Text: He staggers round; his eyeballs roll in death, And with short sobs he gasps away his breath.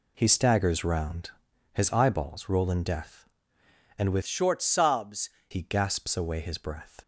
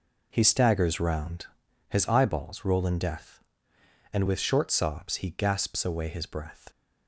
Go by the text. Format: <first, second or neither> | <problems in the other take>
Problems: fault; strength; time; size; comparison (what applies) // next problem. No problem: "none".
second | changes voice from "short" to "sobs"; from 4.2 to 5.3 s; 1.1 s long